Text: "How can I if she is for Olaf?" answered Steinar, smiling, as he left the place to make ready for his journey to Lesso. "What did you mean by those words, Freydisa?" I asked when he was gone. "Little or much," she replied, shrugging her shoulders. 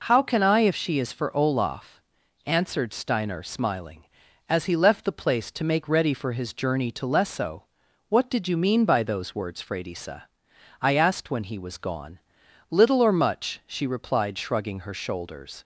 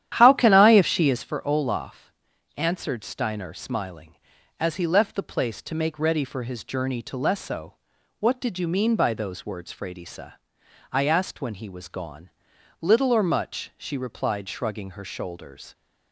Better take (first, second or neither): first